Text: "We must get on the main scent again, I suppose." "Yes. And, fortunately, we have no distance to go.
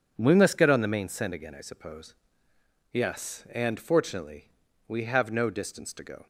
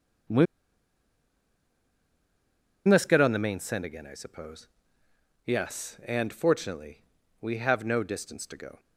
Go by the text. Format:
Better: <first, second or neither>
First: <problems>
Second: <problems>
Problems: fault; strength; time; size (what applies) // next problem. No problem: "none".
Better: first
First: none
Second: pauses between "We" and "must"; strong; at 0.4 s; 2.4 s long